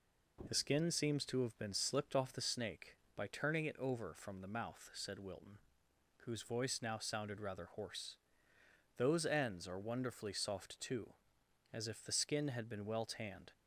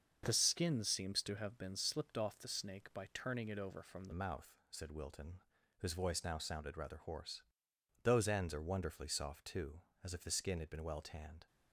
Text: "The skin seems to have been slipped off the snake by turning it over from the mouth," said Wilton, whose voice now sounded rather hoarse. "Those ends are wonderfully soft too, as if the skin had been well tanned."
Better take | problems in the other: first | starts louder than the rest; until 1.2 s; 6.5 dB // changes voice at "mouth"; from 4.1 s on; 7.3 s long

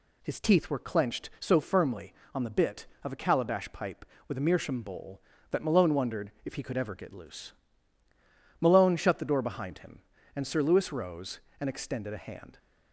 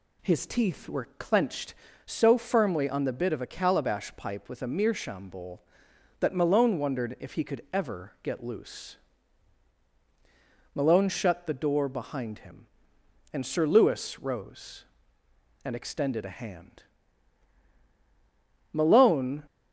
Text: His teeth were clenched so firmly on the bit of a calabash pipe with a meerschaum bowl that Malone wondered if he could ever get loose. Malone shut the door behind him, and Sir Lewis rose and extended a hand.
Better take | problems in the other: first | goes on to say "Malone"; noticeable; from 18.7 s on; 0.72 s long

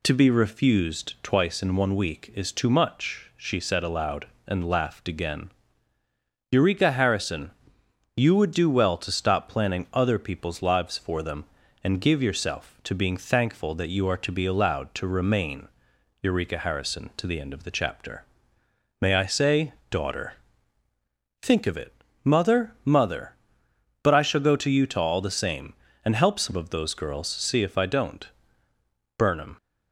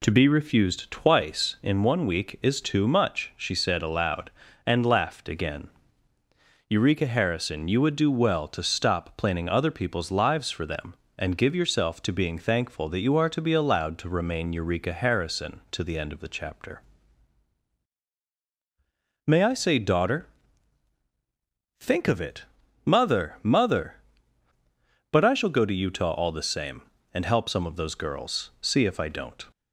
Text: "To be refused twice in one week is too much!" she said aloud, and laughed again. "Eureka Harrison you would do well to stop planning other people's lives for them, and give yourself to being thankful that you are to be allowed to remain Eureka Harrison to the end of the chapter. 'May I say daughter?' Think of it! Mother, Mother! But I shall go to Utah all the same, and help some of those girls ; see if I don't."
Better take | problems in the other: second | pauses between "Harrison" and "you"; noticeable; at 7.4 s; 0.66 s long // pauses between "remain" and "Eureka"; noticeable; at 15.6 s; 0.54 s long // pauses between "say" and "daughter"; slight; at 19.7 s; 0.16 s long // goes on to say "Burnham"; slight; from 29.1 s on; 0.40 s long

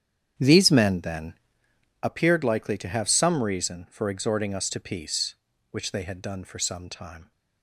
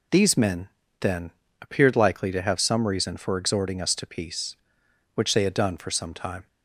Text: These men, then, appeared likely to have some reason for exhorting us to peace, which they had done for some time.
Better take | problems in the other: second | starts louder than the rest; strong; until 2.0 s; 9.5 dB

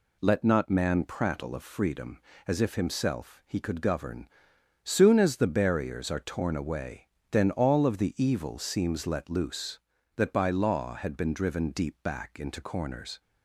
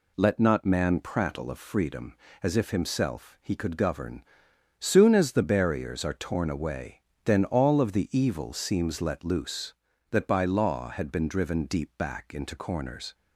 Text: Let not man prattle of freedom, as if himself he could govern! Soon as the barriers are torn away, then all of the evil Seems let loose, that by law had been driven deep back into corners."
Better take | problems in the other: neither | none

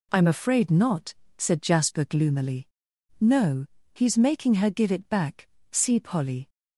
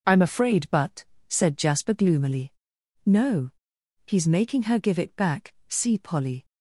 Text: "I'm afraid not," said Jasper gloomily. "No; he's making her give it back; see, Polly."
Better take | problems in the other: first | says "but" for "not"; at 0.7 s

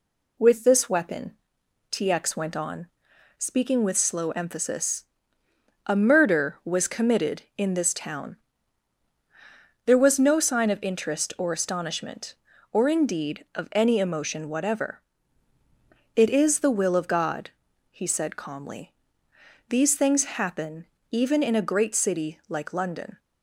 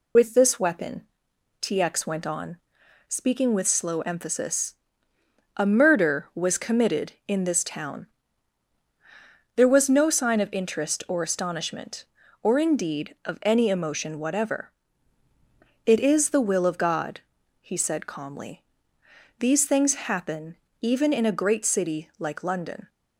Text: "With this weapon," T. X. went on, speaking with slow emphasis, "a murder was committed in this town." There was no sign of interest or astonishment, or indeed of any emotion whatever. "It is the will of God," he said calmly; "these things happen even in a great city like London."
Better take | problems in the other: first | loses the start of "With"; at 0.1 s; 65 ms // pauses between "happen" and "even"; slight; at 20.5 s; 0.24 s long; slight in the first

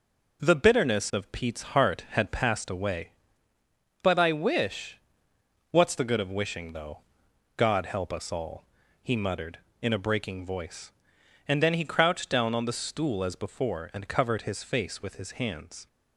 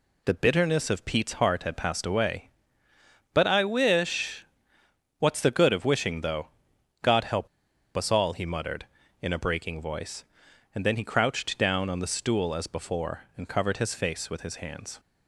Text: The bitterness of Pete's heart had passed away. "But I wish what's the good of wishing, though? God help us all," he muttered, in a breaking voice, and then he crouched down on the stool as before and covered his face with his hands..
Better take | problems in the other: first | pauses between "wish" and "what's"; noticeable; at 4.4 s; 0.74 s long; noticeable in the first // pauses between "help" and "us"; noticeable; at 7.4 s; 0.50 s long

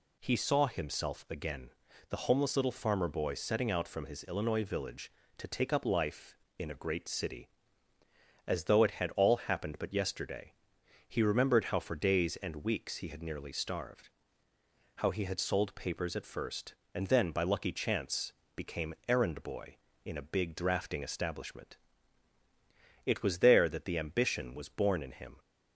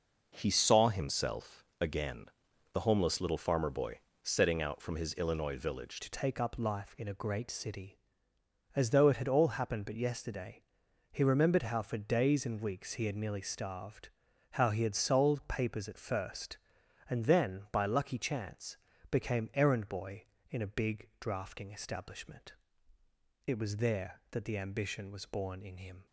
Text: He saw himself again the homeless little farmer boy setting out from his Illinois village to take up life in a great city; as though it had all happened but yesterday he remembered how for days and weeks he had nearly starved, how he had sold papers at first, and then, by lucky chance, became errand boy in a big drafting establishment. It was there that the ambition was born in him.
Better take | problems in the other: first | pauses between "himself" and "again"; slight; at 1.6 s; 0.16 s long // pauses between "again" and "the"; noticeable; at 2.2 s; 0.48 s long; slight in the first // pauses between "boy" and "setting"; slight; at 3.9 s; 0.24 s long // changes voice at "to"; from 6.0 s on; 20.0 s long // pauses between "yesterday" and "he"; noticeable; at 10.6 s; 0.48 s long; noticeable in the first

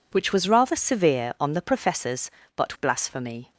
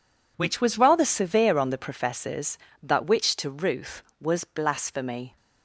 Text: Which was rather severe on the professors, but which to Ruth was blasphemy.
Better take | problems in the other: second | skips "which to Ruth was"; at 2.7 s

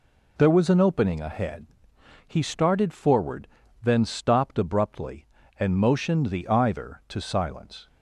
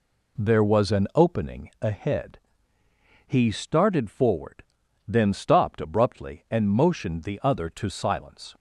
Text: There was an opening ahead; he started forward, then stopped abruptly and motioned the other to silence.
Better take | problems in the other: second | says "either" for "other"; at 6.4 s

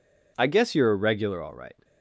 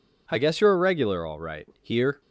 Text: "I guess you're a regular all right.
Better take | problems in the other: first | goes on to say "Here"; slight; from 1.8 s on; 0.38 s long

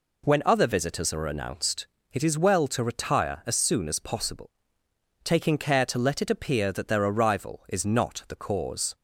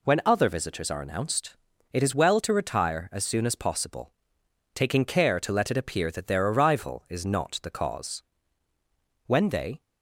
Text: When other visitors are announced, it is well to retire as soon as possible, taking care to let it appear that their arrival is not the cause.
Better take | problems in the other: first | goes on to say "When they"; from 9.2 s on; 0.56 s long

